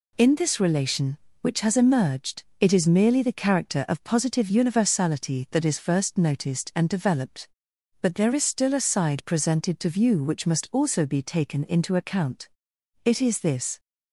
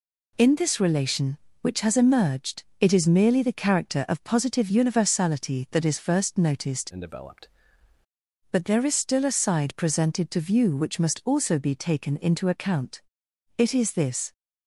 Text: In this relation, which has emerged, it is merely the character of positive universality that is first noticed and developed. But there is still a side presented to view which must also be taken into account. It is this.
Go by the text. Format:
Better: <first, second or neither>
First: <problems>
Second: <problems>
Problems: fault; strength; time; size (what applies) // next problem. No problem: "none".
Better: first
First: none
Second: changes voice from "and" to "developed"; from 6.9 to 7.4 s; 0.5 s long